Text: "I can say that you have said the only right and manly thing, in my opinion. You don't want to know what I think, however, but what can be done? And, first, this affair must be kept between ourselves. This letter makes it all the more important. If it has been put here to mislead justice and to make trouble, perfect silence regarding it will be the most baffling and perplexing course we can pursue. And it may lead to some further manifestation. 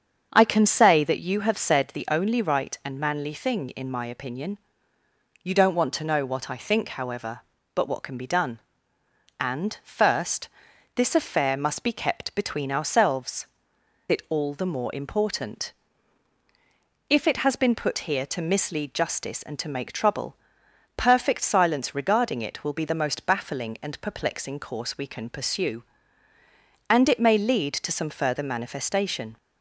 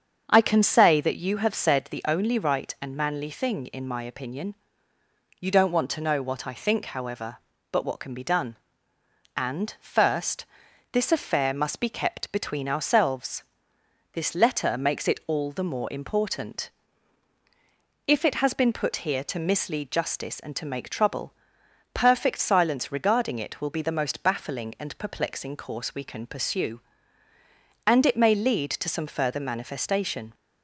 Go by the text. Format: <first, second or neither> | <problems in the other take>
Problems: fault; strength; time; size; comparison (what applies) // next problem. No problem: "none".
second | starts louder than the rest; strong; until 1.3 s; 7 dB; strong in the second // skips "This letter makes"; at 13.7 s